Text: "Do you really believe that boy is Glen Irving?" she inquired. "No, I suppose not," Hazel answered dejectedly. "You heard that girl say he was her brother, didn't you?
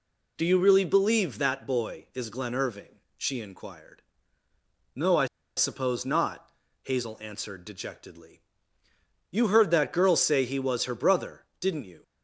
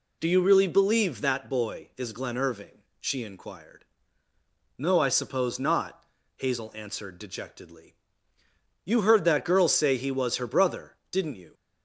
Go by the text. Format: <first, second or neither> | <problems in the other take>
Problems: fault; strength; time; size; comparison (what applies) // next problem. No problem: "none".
second | pauses between "I" and "suppose"; slight; at 5.2 s; 0.29 s long